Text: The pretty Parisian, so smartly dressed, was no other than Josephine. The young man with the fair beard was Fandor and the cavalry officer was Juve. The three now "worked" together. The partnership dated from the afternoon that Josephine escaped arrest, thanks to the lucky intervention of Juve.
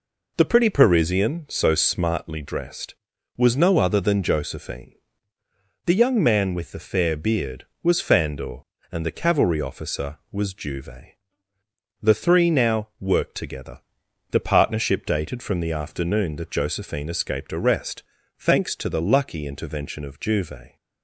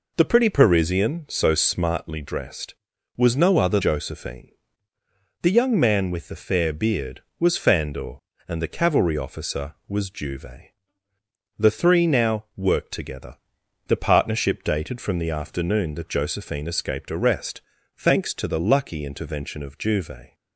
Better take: first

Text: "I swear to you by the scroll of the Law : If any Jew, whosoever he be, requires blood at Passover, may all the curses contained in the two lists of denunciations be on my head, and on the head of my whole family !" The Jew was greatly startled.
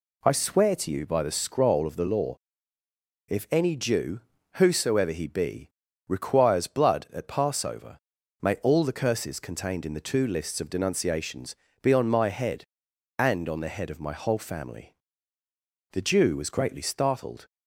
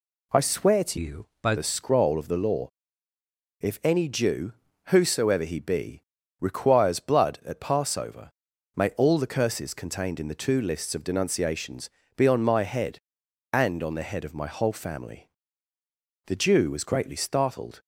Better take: first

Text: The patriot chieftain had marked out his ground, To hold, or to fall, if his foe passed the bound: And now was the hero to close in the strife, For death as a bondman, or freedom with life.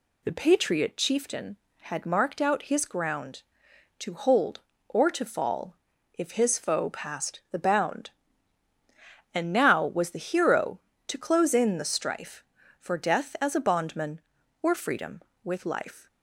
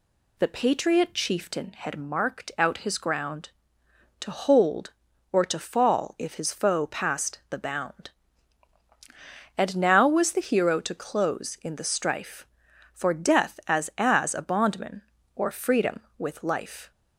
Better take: first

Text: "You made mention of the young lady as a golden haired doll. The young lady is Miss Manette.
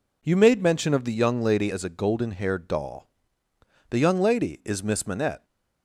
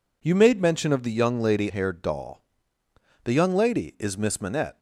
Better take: first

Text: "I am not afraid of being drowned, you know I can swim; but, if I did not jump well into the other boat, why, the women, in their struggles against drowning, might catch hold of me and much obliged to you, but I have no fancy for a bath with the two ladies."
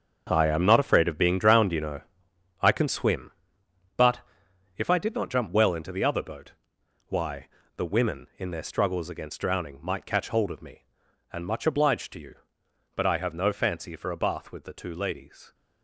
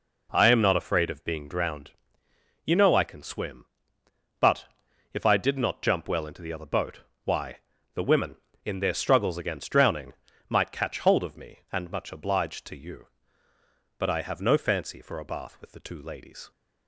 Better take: second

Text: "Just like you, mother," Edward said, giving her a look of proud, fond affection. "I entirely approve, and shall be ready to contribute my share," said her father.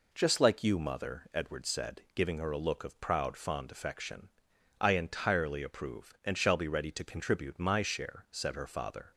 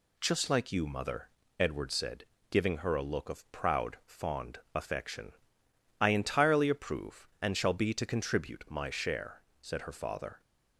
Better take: first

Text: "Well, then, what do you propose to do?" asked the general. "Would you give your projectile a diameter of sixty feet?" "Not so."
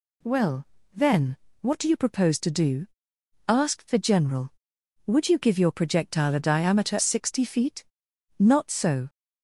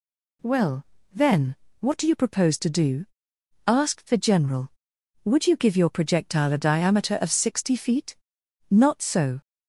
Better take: second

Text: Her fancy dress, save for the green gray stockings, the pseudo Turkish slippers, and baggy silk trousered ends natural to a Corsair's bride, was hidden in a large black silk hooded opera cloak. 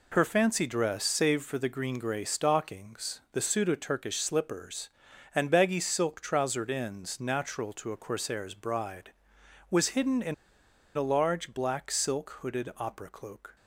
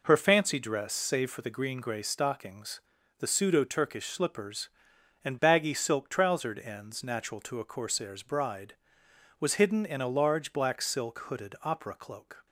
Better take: second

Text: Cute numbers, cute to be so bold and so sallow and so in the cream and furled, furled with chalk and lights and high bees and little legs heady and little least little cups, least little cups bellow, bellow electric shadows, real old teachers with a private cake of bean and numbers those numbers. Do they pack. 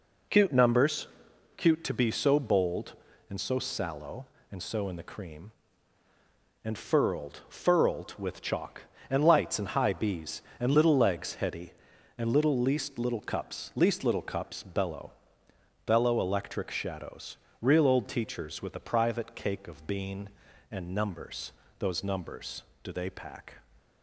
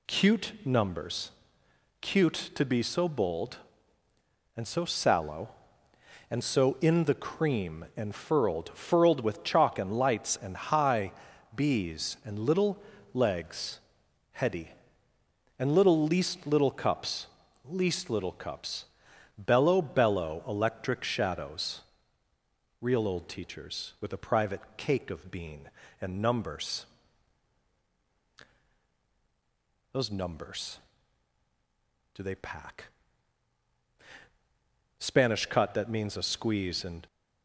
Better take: first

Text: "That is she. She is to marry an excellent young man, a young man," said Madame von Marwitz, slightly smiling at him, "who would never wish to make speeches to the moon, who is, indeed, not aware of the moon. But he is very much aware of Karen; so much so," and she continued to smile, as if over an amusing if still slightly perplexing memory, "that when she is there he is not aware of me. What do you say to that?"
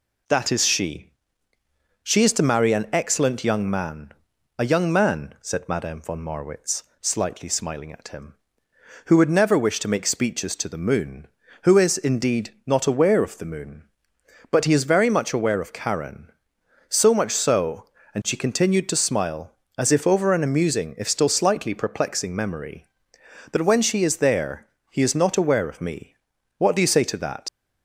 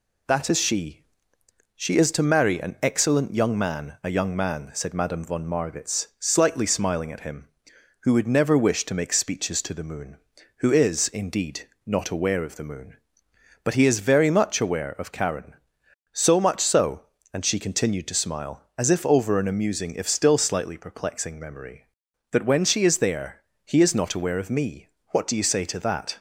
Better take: second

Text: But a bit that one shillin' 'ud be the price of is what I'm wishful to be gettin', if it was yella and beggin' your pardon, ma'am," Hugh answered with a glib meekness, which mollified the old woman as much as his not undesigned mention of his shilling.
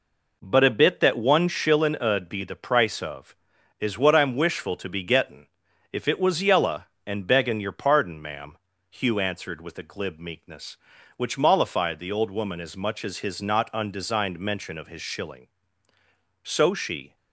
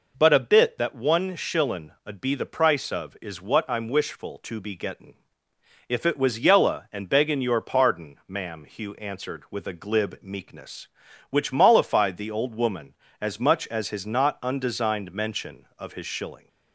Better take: second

